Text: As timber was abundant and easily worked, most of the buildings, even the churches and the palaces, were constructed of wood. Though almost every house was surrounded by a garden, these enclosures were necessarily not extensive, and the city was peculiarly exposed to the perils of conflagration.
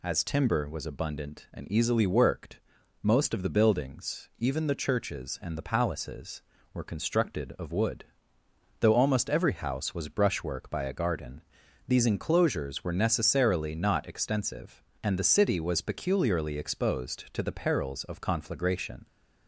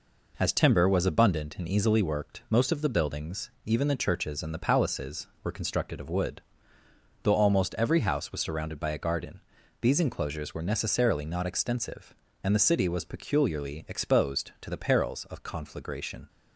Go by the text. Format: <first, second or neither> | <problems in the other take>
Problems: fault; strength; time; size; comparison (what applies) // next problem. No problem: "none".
second | says "brushwork" for "surrounded"; at 10.0 s